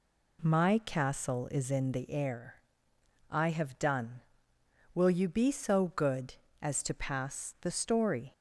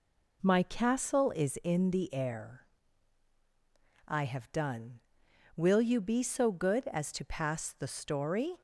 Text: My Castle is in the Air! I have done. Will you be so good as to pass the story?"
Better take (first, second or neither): neither